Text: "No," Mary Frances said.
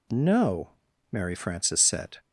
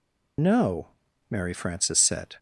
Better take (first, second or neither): first